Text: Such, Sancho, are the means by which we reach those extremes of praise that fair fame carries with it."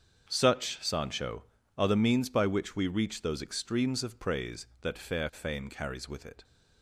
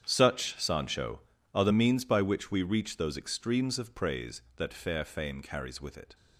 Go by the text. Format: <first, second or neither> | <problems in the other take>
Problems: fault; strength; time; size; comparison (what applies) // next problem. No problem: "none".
first | gets quieter; strong; throughout; 14.5 dB // starts louder than the rest; strong; until 1.0 s; 8.5 dB; strong in the first